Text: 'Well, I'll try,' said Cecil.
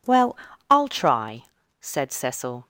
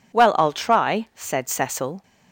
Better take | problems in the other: neither | none

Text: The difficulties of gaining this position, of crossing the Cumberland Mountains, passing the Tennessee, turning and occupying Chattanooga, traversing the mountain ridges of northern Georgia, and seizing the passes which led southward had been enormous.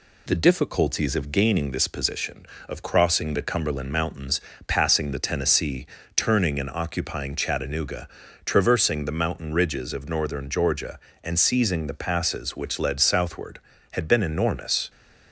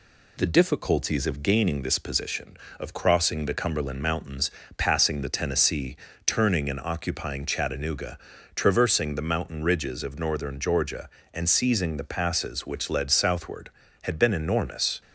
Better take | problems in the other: neither | none

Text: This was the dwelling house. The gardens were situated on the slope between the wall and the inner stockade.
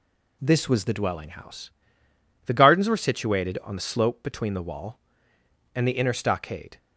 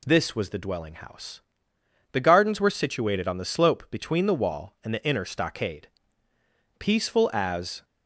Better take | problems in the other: first | goes on to say "Peaceful as"; noticeable; from 6.7 s on; 1.0 s long

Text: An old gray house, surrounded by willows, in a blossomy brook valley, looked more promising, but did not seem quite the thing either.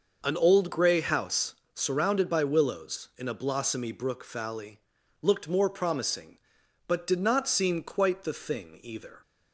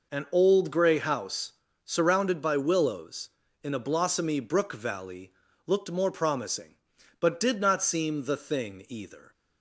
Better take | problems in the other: first | skips "quite"; at 8.2 s

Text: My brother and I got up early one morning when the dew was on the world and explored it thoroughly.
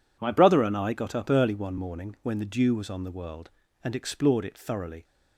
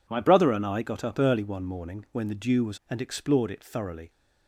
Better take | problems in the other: first | skips "on the world"; at 2.8 s

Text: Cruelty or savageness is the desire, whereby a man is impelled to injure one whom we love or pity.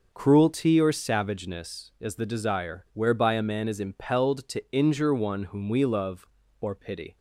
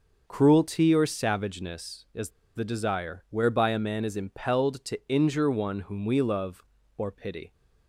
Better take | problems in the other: first | pauses between "is" and "the"; slight; at 2.3 s; 0.25 s long

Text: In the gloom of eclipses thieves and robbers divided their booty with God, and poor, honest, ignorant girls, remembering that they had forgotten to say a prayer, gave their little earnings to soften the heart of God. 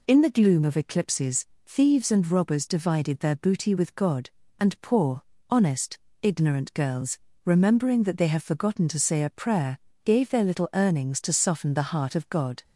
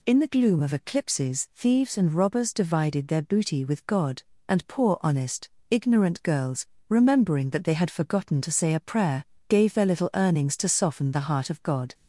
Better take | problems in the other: second | pauses between "eclipses" and "thieves"; slight; at 1.4 s; 0.20 s long // says "have" for "had"; at 8.2 s

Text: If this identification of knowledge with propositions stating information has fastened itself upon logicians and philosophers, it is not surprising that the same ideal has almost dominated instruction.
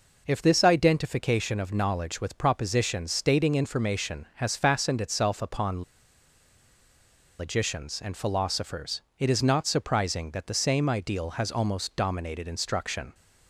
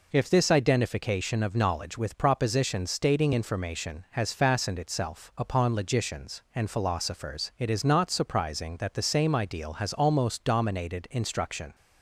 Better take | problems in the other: second | pauses between "upon" and "logicians"; strong; at 5.8 s; 1.5 s long

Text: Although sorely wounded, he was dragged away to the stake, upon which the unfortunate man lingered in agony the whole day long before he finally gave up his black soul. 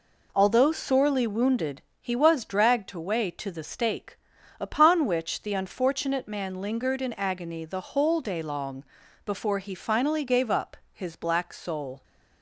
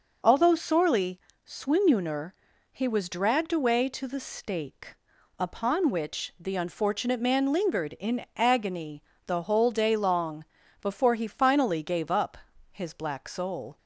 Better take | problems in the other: first | says "swinuner" for "wounded"; at 1.4 s // pauses between "agony" and "the"; slight; at 9.0 s; 0.24 s long // pauses between "long" and "before"; slight; at 10.4 s; 0.36 s long; also in the first // pauses between "up" and "his"; slight; at 12.3 s; 0.34 s long; slight in the first

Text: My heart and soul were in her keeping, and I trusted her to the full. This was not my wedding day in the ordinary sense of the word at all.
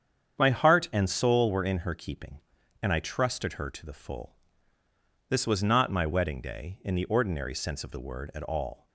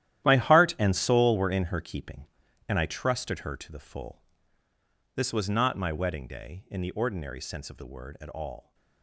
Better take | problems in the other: first | gets quieter; strong; throughout; 13.5 dB // starts louder than the rest; strong; until 1.2 s; 12.5 dB; strong in the first

